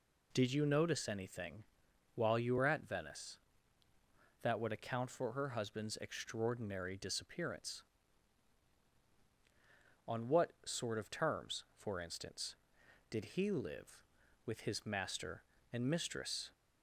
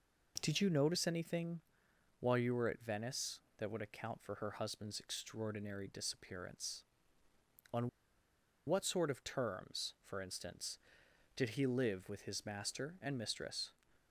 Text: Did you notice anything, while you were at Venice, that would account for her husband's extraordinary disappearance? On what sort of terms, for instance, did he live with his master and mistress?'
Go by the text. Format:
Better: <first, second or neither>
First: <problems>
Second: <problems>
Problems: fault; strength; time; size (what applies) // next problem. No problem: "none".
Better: first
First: none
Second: pauses between "On" and "what"; noticeable; at 7.8 s; 0.78 s long